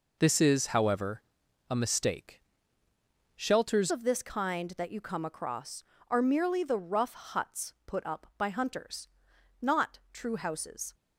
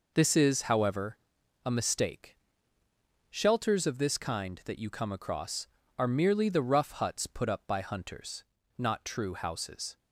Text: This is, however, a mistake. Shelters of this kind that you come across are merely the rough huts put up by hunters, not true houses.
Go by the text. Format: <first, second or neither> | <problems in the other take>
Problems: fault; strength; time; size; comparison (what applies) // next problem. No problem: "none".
second | changes voice at "of"; from 3.8 s on; 7.1 s long